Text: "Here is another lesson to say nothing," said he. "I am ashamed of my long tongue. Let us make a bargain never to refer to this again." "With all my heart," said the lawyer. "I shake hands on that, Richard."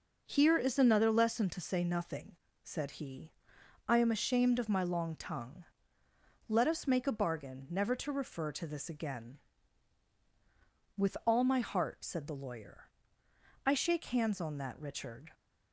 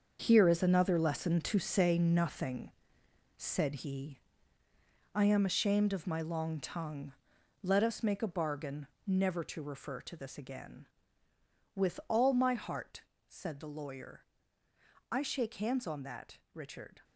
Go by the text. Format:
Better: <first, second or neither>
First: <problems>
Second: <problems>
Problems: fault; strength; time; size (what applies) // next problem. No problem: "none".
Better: first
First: none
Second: gets quieter; strong; throughout; 10.5 dB // pauses between "bargain" and "never"; slight; at 8.8 s; 0.20 s long